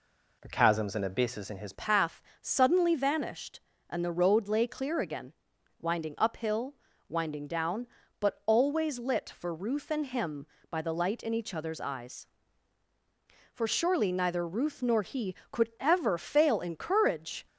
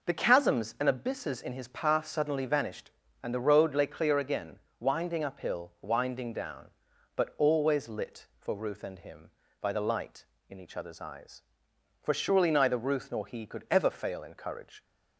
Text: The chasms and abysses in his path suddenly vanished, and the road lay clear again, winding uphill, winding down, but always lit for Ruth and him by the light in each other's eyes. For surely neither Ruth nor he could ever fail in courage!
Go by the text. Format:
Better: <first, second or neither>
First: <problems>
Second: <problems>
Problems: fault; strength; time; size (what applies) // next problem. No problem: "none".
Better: second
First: changes voice at "path"; from 1.7 s on; 15.7 s long // pauses between "path" and "suddenly"; slight; at 2.2 s; 0.20 s long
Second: none